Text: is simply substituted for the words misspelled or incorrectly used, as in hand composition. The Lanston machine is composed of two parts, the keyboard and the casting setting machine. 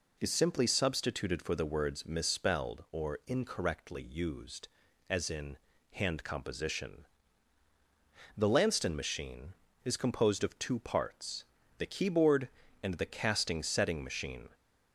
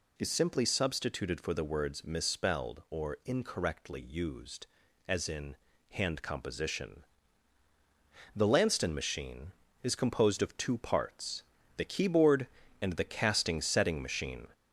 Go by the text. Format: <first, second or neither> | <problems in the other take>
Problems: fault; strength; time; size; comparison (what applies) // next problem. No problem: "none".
first | gets louder; slight; throughout; 2.5 dB // pauses between "in" and "hand"; slight; at 5.5 s; 0.34 s long; slight in the first